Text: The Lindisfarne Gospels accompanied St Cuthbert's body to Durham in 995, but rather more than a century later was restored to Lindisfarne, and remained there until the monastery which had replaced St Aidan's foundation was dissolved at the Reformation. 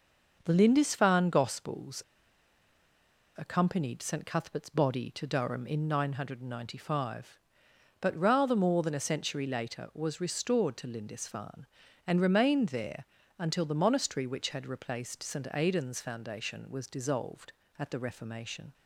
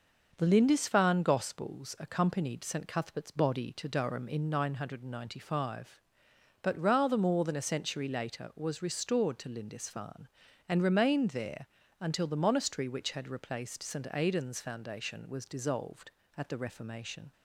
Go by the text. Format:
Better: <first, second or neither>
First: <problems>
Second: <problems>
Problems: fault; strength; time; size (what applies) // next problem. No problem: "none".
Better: second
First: starts louder than the rest; noticeable; until 1.4 s; 6 dB // pauses between "Gospels" and "accompanied"; strong; at 2.0 s; 1.3 s long // pauses between "there" and "until"; slight; at 13.0 s; 0.34 s long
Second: starts louder than the rest; noticeable; until 1.3 s; 6 dB // pauses between "there" and "until"; slight; at 11.6 s; 0.34 s long